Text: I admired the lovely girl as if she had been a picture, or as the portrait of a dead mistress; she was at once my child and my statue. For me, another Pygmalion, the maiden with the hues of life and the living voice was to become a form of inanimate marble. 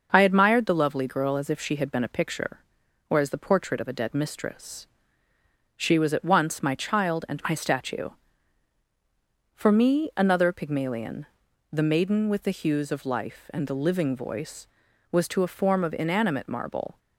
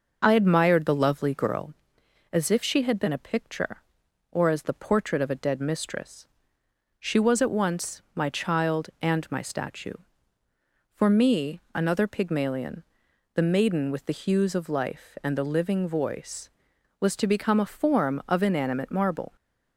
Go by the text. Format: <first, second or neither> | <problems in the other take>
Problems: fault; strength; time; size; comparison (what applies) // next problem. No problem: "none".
second | starts louder than the rest; until 1.1 s; 6.5 dB // skips "become"; at 15.4 s